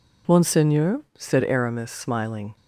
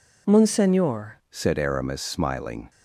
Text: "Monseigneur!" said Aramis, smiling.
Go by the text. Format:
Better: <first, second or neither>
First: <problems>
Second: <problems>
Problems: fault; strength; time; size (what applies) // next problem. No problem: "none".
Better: first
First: none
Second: changes voice at "said"; from 1.2 s on; 1.4 s long